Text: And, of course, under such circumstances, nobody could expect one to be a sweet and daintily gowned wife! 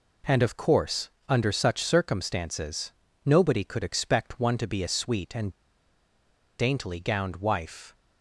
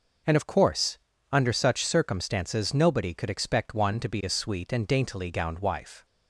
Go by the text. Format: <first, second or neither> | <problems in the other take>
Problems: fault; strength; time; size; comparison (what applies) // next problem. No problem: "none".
second | pauses between "and" and "daintily"; at 5.5 s; 1.0 s long